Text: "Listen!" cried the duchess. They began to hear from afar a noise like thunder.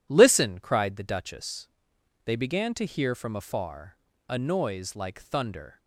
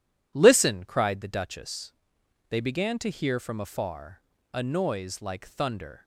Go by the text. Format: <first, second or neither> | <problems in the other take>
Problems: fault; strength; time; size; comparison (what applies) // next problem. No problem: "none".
neither | pauses between "afar" and "a"; slight; the same in both